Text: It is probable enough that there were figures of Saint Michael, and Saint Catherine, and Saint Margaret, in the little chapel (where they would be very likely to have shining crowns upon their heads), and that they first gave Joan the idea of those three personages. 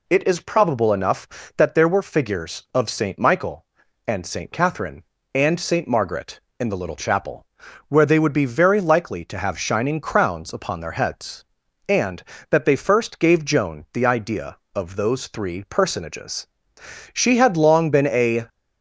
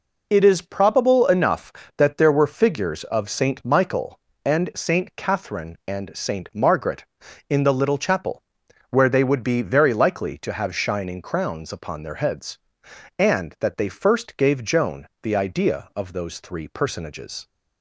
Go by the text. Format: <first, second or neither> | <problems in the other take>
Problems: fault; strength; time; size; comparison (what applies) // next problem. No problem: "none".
second | goes on to say "She had long been a"; from 17.1 s on; 1.3 s long